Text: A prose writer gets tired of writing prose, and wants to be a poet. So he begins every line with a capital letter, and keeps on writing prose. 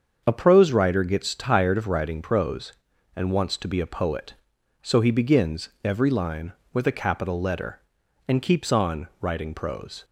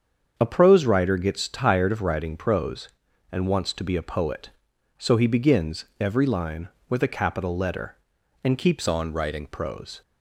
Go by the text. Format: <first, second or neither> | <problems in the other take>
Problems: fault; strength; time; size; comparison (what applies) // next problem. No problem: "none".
first | starts louder than the rest; strong; until 1.3 s; 7 dB; also in the first // changes voice from "on" to "writing"; from 8.8 to 9.4 s; 0.6 s long